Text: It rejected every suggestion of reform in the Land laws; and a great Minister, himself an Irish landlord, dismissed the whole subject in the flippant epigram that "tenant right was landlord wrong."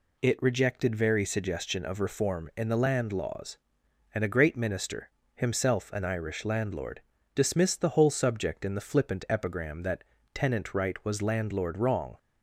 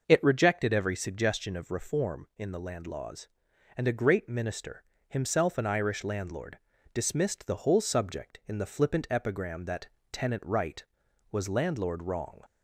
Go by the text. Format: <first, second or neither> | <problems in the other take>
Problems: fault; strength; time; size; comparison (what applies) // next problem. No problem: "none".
second | says "very" for "every"; at 0.9 s // pauses between "that" and "tenant"; slight; at 10.0 s; 0.30 s long; slight in the second